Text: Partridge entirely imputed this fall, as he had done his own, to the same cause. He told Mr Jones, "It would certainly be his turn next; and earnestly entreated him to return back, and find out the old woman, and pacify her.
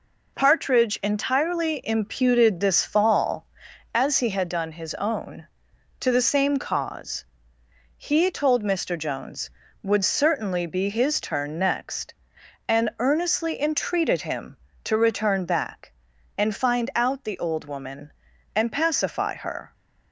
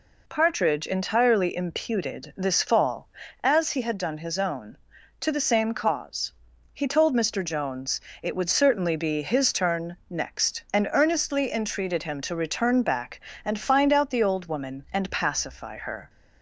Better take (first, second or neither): second